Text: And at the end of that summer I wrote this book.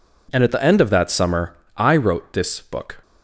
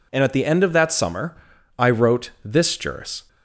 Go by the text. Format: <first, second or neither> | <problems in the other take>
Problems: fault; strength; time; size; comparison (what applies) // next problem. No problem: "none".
first | pauses between "summer" and "I"; at 1.3 s; 0.40 s long; slight in the first // says "juris" for "book"; at 2.7 s